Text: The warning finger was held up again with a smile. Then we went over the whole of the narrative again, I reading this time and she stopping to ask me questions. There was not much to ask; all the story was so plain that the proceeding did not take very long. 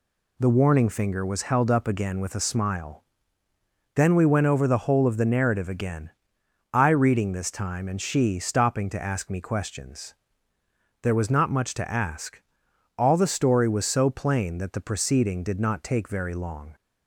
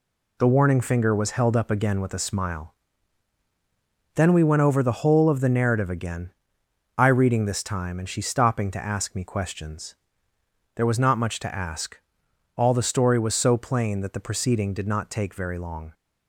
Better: neither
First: none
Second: none

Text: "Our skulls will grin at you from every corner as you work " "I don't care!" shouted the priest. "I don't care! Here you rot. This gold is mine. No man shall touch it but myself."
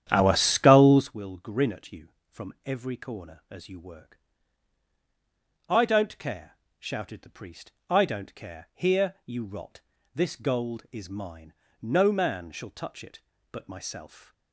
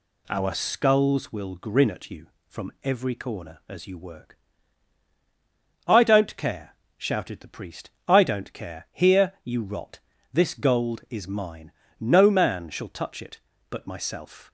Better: second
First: starts louder than the rest; strong; until 1.1 s; 10.5 dB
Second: none

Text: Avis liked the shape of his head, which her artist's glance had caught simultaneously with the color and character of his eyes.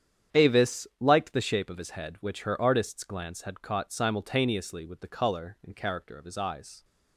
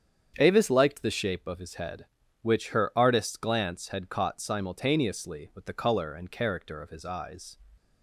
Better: neither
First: starts louder than the rest; strong; until 1.4 s; 9 dB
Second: starts louder than the rest; strong; until 1.3 s; 8 dB

